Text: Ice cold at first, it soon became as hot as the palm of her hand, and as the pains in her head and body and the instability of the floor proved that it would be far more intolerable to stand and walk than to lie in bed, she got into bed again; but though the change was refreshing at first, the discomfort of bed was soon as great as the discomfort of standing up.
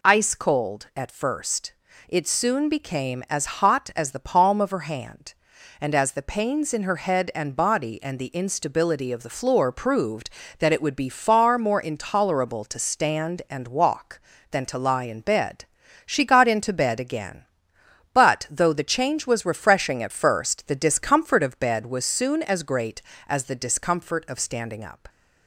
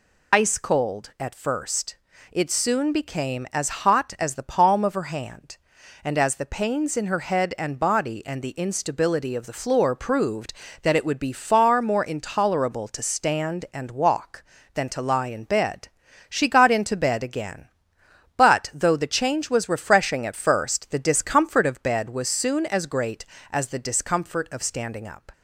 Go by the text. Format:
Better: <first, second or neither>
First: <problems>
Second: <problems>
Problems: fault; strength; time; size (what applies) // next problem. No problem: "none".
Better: first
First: none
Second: loses the start of "Ice"; at 0.3 s; 65 ms